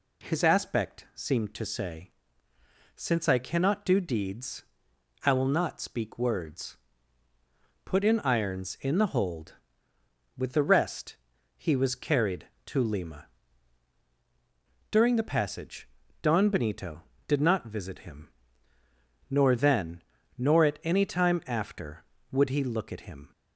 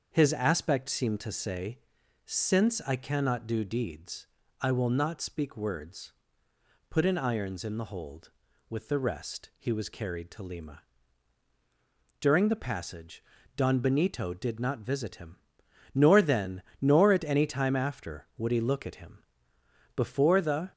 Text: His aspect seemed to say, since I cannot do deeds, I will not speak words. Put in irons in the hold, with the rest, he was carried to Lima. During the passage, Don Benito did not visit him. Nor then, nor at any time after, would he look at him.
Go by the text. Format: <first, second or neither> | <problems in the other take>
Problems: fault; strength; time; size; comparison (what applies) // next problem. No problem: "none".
first | starts louder than the rest; until 1.1 s; 6.5 dB // goes on to say "Before the"; noticeable; from 19.9 s on; 0.76 s long